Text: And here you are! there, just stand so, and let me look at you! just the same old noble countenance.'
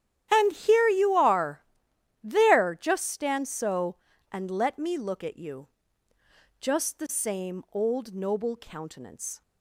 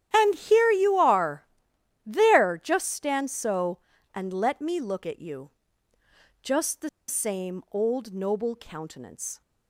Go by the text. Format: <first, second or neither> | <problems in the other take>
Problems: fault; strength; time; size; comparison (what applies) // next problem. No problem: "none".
first | starts louder than the rest; strong; until 1.1 s; 11 dB; strong in the first // pauses between "the" and "same"; slight; at 6.8 s; 0.19 s long